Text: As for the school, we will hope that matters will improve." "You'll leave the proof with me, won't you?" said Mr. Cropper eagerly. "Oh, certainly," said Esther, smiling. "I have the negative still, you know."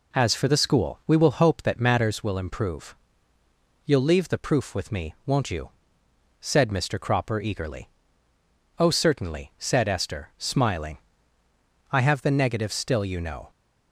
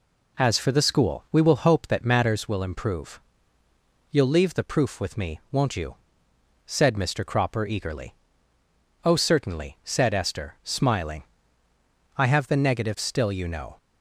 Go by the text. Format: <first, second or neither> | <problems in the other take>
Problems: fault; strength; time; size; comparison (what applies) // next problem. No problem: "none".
neither | none